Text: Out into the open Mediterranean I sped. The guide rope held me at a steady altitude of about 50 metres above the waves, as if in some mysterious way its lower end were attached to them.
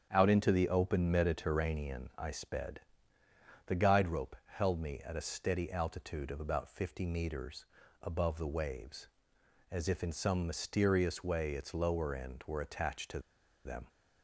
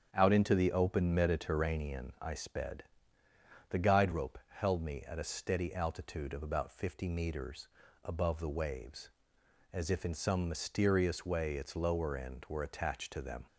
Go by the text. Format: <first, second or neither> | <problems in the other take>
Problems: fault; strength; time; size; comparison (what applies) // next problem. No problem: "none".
second | starts louder than the rest; strong; until 1.1 s; 8.5 dB; strong in the second // pauses between "metres" and "above"; slight; at 7.6 s; 0.36 s long; slight in the second // pauses between "to" and "them"; noticeable; at 13.1 s; 0.46 s long